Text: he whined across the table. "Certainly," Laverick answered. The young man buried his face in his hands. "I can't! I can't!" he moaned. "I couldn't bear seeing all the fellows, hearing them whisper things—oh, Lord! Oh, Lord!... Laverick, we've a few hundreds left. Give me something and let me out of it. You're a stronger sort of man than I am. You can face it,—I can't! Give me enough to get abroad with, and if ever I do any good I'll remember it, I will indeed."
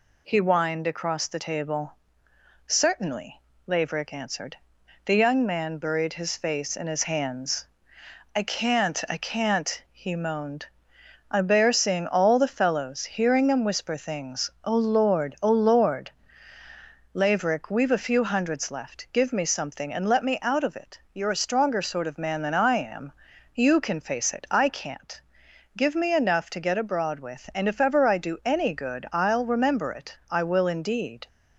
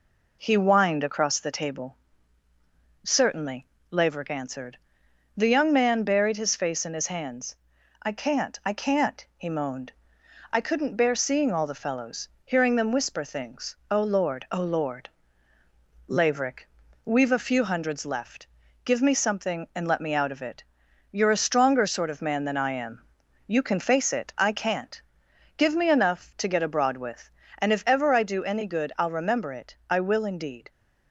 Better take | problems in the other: second | skips "couldn't"; at 11.4 s

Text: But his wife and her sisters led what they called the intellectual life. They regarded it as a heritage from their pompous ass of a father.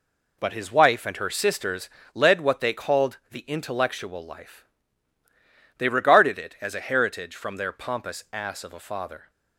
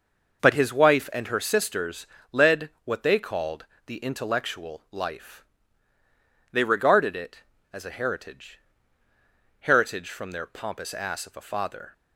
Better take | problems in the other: first | pauses between "sisters" and "led"; slight; at 2.0 s; 0.26 s long; slight in the first // pauses between "called" and "the"; slight; at 3.6 s; 0.22 s long // says "heritage" twice; at 9.6 s

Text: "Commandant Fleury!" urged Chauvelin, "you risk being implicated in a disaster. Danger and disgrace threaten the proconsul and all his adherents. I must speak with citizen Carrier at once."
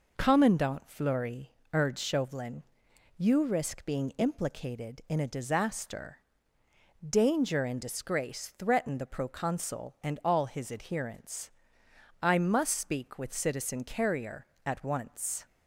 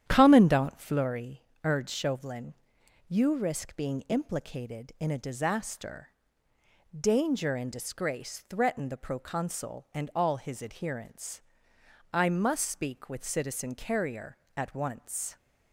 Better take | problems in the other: first | starts louder than the rest; strong; until 1.1 s; 10 dB

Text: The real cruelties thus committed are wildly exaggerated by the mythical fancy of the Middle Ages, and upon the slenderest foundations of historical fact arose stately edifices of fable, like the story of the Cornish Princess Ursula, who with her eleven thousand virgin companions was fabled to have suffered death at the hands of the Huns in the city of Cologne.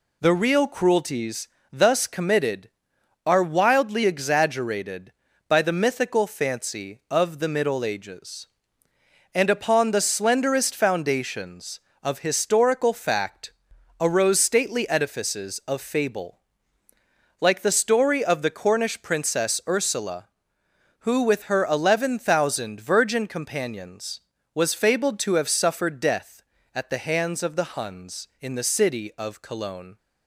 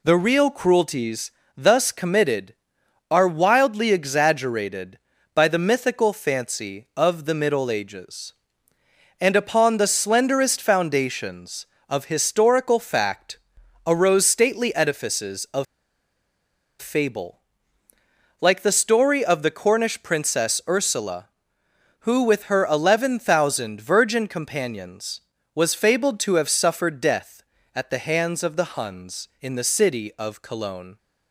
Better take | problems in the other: first | pauses between "cruelties" and "thus"; slight; at 1.3 s; 0.26 s long; slight in the first // pauses between "fact" and "arose"; noticeable; at 13.3 s; 0.46 s long; noticeable in the first // pauses between "of" and "fable"; at 15.6 s; 1.1 s long

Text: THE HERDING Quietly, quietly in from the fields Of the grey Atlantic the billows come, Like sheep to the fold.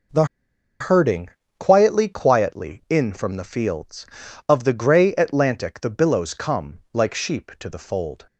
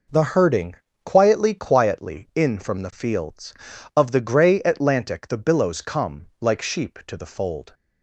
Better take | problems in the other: second | pauses between "THE" and "HERDING"; noticeable; at 0.2 s; 0.55 s long // pauses between "HERDING" and "Quietly"; slight; at 1.2 s; 0.30 s long; slight in the second

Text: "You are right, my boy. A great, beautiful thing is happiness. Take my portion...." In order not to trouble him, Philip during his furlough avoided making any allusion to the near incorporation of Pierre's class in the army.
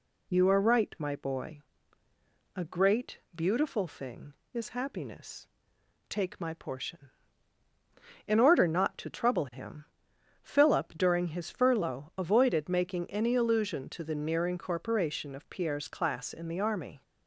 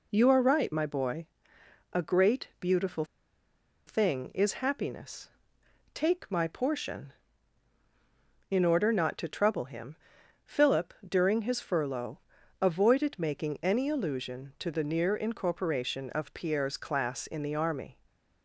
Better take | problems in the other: first | pauses between "beautiful" and "thing"; noticeable; at 3.0 s; 0.83 s long // pauses between "Philip" and "during"; slight; at 10.9 s; 0.16 s long // pauses between "furlough" and "avoided"; at 12.1 s; 0.42 s long

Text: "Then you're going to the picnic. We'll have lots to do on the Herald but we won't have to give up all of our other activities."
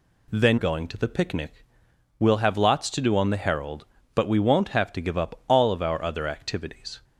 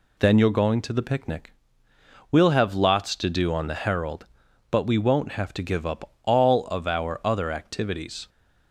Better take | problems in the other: second | skips "you're"; at 0.5 s

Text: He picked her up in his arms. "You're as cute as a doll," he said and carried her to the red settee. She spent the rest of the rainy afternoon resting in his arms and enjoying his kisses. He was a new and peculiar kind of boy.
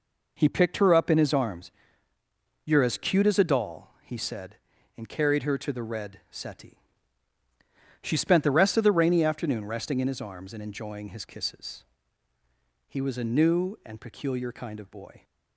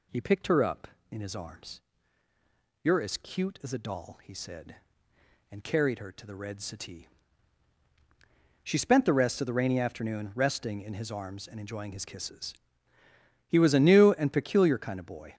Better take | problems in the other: neither | none

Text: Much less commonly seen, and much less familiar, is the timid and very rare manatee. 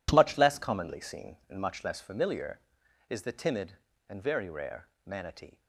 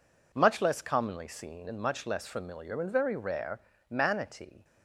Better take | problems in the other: first | skips "is the timid"; at 2.7 s // pauses between "rare" and "manatee"; slight; at 3.5 s; 0.30 s long; slight in the first

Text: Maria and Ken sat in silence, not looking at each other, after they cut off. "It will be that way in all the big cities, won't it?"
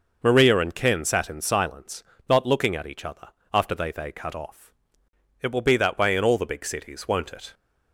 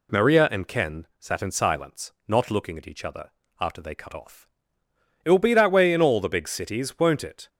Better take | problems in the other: second | says "they" twice; at 3.9 s

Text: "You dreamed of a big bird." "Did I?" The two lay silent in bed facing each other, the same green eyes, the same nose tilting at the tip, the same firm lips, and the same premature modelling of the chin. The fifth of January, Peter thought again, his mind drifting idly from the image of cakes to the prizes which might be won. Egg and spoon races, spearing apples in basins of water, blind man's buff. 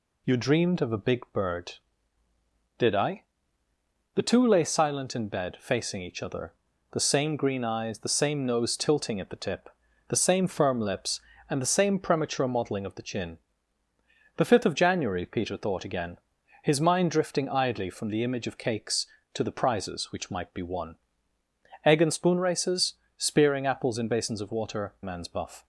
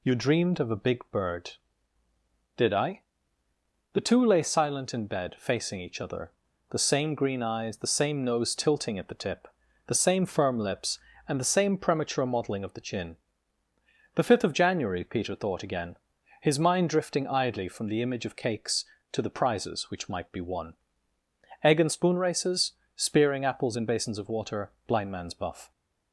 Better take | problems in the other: second | skips "blind"; at 24.9 s

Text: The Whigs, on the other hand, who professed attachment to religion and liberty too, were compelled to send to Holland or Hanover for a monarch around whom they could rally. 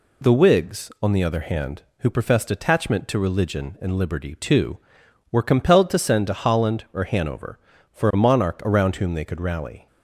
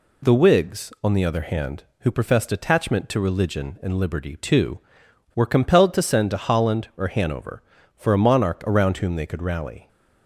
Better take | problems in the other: neither | none

